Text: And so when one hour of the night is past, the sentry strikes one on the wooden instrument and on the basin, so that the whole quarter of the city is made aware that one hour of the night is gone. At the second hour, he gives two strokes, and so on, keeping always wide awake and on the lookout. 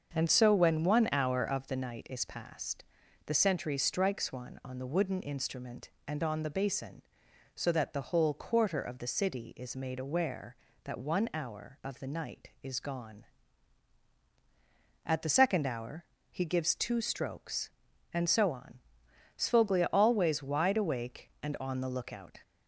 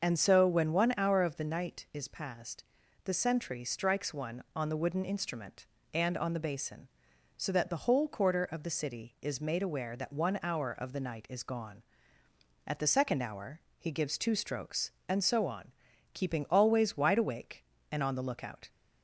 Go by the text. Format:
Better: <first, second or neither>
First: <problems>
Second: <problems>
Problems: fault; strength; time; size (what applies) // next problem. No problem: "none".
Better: second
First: starts louder than the rest; until 1.1 s; 6.5 dB // says "sfoglia" for "keeping"; at 19.3 s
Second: starts louder than the rest; until 1.0 s; 6.5 dB